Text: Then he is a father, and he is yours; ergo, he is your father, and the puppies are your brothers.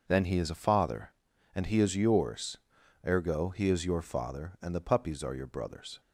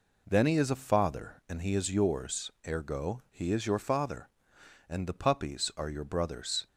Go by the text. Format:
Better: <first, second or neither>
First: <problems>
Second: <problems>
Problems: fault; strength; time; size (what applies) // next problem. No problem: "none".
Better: neither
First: none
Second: none